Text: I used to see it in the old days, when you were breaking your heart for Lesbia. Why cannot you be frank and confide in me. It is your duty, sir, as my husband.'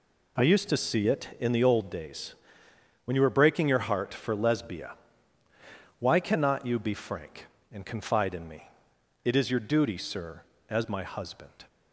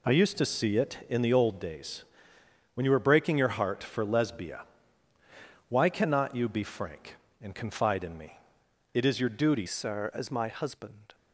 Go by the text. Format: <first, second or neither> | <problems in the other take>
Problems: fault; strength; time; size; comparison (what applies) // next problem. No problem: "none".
first | changes voice at "sir"; from 9.6 s on; 1.5 s long